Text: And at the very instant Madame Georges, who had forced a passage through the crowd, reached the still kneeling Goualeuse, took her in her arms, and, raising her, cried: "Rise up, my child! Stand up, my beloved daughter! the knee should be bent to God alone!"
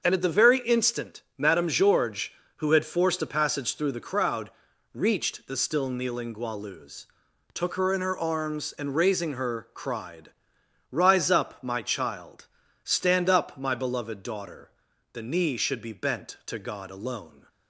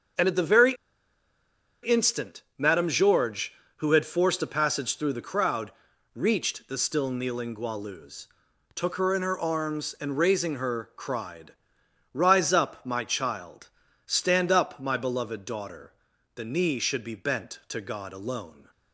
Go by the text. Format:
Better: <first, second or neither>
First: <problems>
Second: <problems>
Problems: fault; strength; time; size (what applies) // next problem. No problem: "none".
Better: first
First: starts louder than the rest; until 1.0 s; 7 dB // pauses between "instant" and "Madame"; slight; at 1.2 s; 0.16 s long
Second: starts louder than the rest; until 2.2 s; 7 dB // pauses between "very" and "instant"; at 0.7 s; 1.0 s long // pauses between "instant" and "Madame"; slight; at 2.4 s; 0.16 s long